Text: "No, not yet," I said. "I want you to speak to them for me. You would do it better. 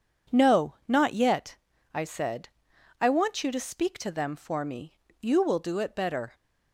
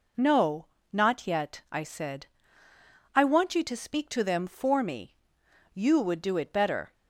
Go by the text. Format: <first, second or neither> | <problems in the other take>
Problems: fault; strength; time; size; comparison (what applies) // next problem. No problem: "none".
second | says "will" for "would"; at 5.4 s